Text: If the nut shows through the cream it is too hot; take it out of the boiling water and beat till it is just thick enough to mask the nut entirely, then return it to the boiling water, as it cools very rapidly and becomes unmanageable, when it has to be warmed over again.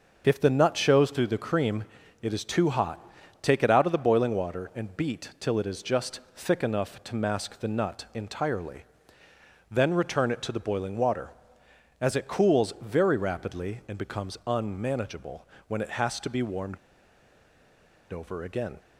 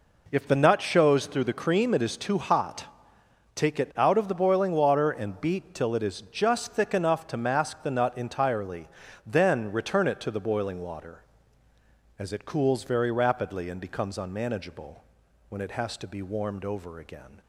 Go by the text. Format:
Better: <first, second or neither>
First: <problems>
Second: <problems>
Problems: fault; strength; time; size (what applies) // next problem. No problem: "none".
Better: second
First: starts louder than the rest; until 1.2 s; 6.5 dB // pauses between "cream" and "it"; slight; at 1.8 s; 0.36 s long // pauses between "just" and "thick"; slight; at 6.1 s; 0.16 s long // pauses between "warmed" and "over"; strong; at 16.7 s; 1.3 s long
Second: none